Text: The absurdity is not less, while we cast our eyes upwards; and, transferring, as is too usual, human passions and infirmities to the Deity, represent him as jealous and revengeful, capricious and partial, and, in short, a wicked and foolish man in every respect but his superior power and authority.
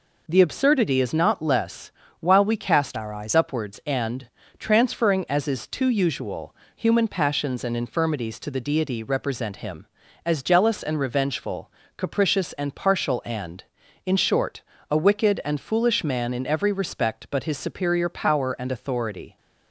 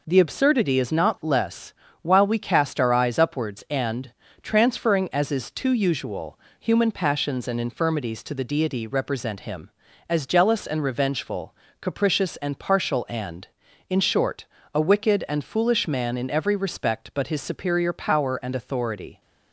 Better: second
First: changes voice from "our" to "eyes"; from 2.9 to 3.3 s; 0.4 s long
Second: none

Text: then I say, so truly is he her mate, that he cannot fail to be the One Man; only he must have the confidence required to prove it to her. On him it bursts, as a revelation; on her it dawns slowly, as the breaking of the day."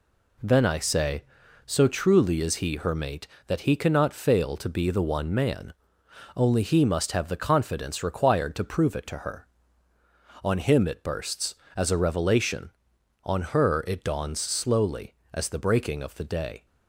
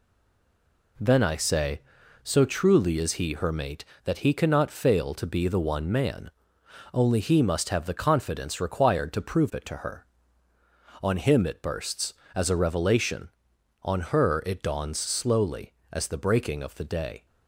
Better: first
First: none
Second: stays silent before the first word; slight; until 0.9 s; 0.9 s long

